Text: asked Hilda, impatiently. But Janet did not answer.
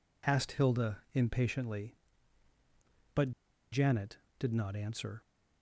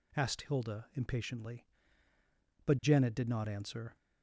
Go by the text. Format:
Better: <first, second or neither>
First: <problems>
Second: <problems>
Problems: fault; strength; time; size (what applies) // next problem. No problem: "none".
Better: second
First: pauses between "But" and "Janet"; at 3.3 s; 0.41 s long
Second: none